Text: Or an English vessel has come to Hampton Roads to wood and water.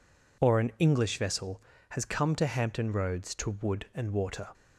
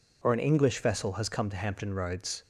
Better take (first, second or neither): first